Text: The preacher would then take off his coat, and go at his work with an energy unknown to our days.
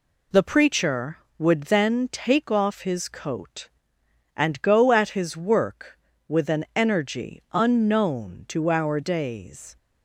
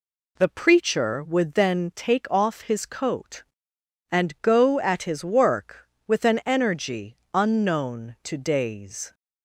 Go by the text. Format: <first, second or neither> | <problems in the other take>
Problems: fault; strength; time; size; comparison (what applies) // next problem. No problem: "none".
first | pauses between "energy" and "unknown"; slight; at 7.1 s; 0.16 s long // skips "our"; at 8.3 s